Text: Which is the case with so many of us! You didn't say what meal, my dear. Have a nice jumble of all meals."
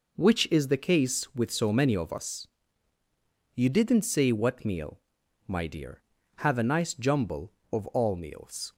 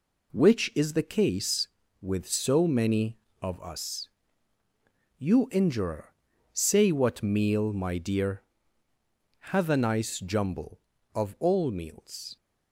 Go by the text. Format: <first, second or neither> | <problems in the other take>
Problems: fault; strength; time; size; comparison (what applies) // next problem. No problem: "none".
first | says "injurer" for "didn't"; at 5.4 s